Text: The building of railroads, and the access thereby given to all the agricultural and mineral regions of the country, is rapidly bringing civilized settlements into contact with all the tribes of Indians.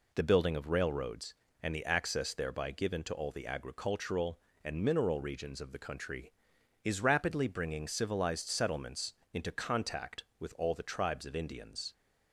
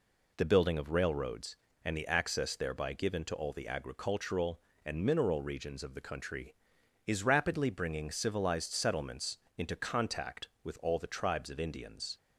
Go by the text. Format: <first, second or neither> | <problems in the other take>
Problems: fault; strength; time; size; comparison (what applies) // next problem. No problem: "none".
neither | pauses between "settlements" and "into"; slight; the same in both